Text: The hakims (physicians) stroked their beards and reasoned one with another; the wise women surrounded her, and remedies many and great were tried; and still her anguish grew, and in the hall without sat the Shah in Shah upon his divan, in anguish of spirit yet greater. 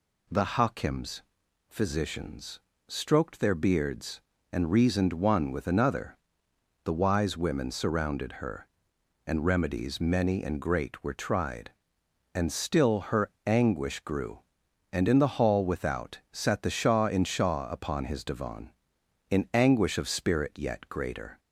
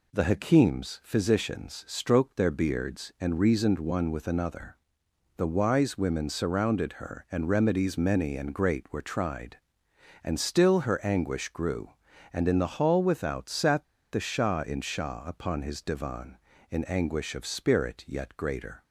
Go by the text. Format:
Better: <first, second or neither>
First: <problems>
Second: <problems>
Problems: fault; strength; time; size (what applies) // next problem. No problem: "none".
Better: first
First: none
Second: pauses between "sat" and "the"; slight; at 13.8 s; 0.27 s long